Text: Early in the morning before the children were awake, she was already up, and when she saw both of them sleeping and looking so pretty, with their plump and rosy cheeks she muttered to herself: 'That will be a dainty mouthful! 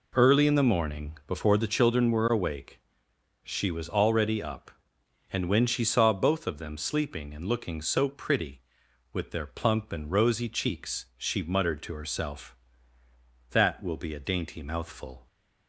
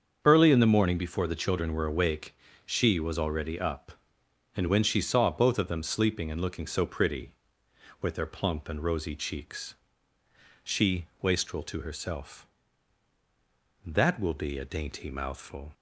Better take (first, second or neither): first